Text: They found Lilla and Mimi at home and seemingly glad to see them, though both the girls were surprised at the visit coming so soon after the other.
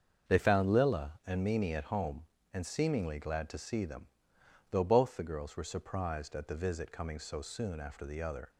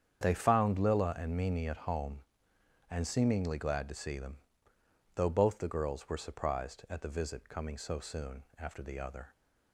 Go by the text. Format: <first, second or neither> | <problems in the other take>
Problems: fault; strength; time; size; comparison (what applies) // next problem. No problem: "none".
neither | starts louder than the rest; the same in both